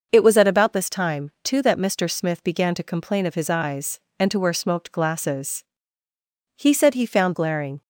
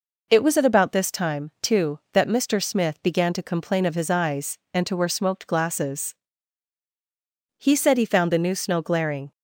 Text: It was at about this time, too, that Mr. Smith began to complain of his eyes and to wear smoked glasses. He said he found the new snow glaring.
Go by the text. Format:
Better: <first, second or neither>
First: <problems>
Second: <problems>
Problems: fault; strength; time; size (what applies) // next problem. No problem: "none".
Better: second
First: starts louder than the rest; noticeable; until 1.1 s; 6 dB // skips "the new snow"; at 7.3 s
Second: none